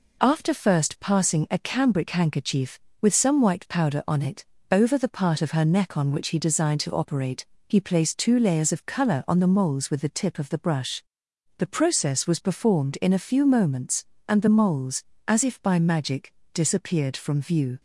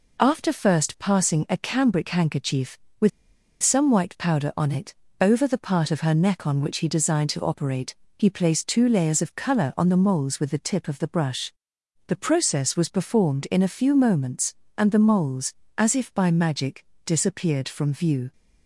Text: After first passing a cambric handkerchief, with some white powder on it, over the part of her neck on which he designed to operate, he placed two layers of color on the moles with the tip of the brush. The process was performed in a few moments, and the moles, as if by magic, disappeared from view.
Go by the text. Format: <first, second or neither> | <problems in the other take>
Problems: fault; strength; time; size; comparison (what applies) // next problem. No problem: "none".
first | pauses between "with" and "some"; noticeable; at 3.0 s; 0.52 s long